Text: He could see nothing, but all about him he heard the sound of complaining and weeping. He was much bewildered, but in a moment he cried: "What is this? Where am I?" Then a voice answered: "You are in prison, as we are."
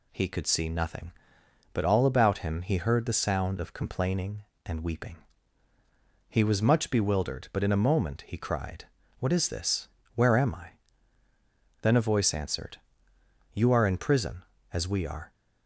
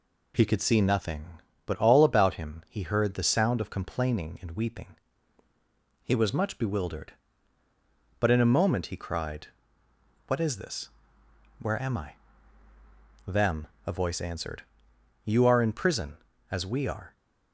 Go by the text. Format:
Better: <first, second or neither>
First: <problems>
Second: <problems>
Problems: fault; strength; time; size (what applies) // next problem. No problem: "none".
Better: first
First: none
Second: says "Them" for "Then"; at 13.2 s